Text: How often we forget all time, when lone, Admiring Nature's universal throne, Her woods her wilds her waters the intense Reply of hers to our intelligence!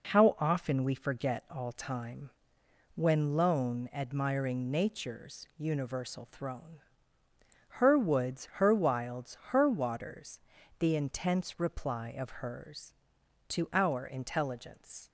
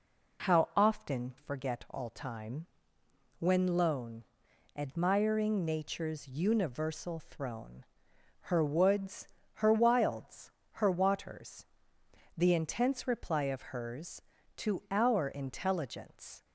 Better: first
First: pauses between "waters" and "the"; at 10.3 s; 0.38 s long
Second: skips "we"; at 1.3 s // pauses between "woods" and "her"; slight; at 9.2 s; 0.28 s long // pauses between "wilds" and "her"; slight; at 10.5 s; 0.28 s long // pauses between "waters" and "the"; noticeable; at 11.6 s; 0.72 s long

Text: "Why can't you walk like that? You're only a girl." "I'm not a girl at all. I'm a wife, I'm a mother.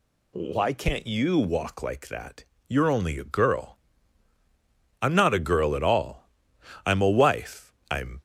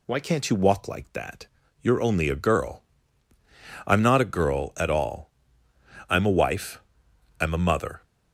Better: second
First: stops before "a mother"; at 8.1 s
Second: none

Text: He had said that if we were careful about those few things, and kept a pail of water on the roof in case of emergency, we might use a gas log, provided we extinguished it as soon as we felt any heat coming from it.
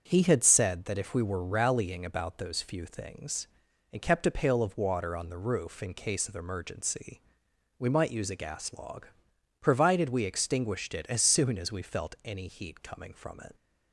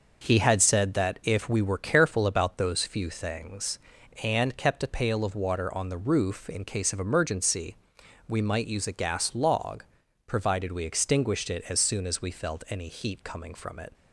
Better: second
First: starts louder than the rest; until 1.0 s; 6 dB // says "rallying" for "careful"; at 1.4 s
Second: none

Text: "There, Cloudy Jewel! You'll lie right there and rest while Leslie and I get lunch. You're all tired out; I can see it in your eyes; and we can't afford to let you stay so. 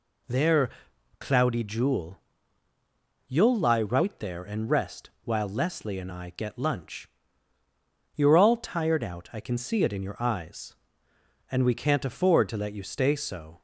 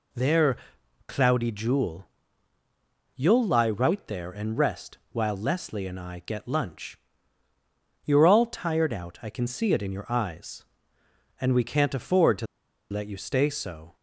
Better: first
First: pauses between "rest" and "while"; slight; at 5.0 s; 0.16 s long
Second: pauses between "rest" and "while"; slight; at 4.9 s; 0.16 s long // pauses between "to" and "let"; at 12.4 s; 0.45 s long

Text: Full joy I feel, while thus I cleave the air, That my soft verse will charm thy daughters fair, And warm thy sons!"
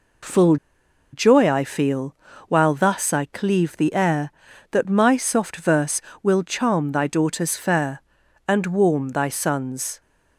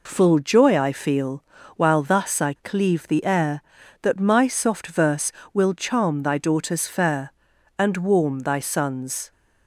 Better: second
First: pauses between "Full" and "joy"; noticeable; at 0.5 s; 0.57 s long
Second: none

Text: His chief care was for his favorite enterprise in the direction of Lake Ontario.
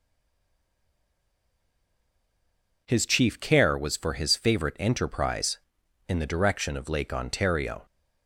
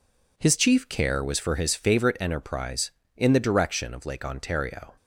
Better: second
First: stays silent before the first word; strong; until 2.8 s; 2.8 s long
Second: none

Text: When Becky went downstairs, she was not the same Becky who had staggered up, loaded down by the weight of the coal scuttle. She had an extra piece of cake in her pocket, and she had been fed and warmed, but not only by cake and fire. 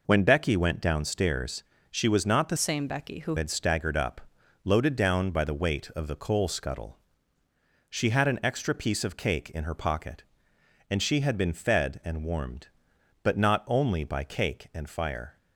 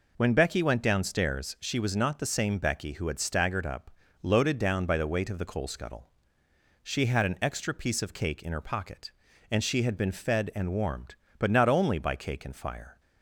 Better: second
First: changes voice from "same" to "who"; from 2.5 to 3.3 s; 0.8 s long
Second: none

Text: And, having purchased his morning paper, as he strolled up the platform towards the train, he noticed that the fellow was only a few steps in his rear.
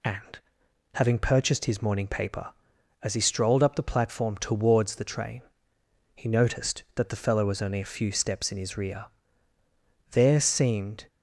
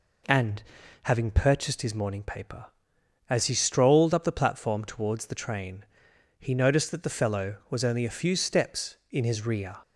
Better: second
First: goes on to say "There seemed"; noticeable; from 10.1 s on; 0.94 s long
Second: none

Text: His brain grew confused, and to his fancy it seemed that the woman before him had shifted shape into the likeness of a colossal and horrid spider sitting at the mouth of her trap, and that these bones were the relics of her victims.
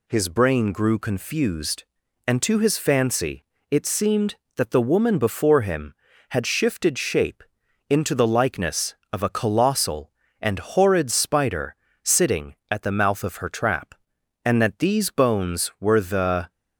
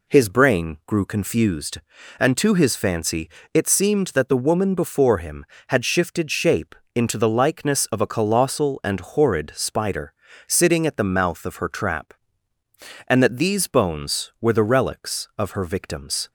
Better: second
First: pauses between "fancy" and "it"; slight; at 3.4 s; 0.26 s long // pauses between "shape" and "into"; noticeable; at 7.4 s; 0.48 s long // pauses between "spider" and "sitting"; slight; at 11.7 s; 0.28 s long // stops before "relics of her victims"; at 16.5 s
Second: pauses between "fancy" and "it"; slight; at 3.2 s; 0.24 s long // pauses between "shape" and "into"; slight; at 6.7 s; 0.20 s long // pauses between "spider" and "sitting"; slight; at 10.1 s; 0.34 s long

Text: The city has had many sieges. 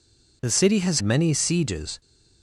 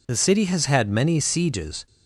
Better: second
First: skips "had"; at 1.0 s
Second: none

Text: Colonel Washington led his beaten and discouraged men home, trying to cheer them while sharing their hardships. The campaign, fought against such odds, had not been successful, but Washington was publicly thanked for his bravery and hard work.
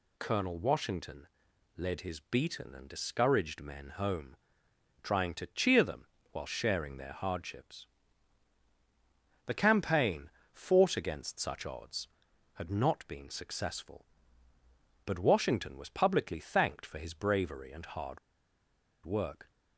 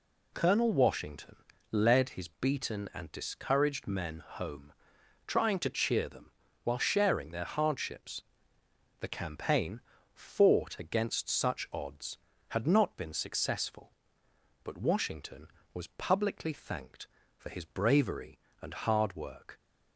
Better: second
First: pauses between "Washington" and "led"; noticeable; at 1.2 s; 0.50 s long // pauses between "them" and "while"; slight; at 6.0 s; 0.26 s long // pauses between "hard" and "work"; noticeable; at 18.1 s; 0.86 s long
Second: pauses between "Washington" and "led"; slight; at 1.3 s; 0.34 s long // pauses between "them" and "while"; slight; at 6.3 s; 0.32 s long

